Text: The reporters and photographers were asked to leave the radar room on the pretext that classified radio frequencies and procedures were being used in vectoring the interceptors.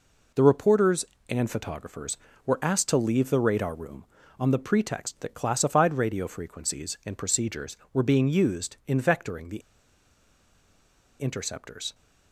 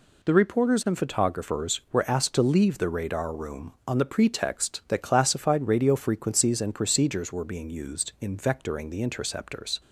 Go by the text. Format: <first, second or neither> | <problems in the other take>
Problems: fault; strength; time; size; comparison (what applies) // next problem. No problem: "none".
second | pauses between "the" and "interceptors"; strong; at 9.5 s; 1.6 s long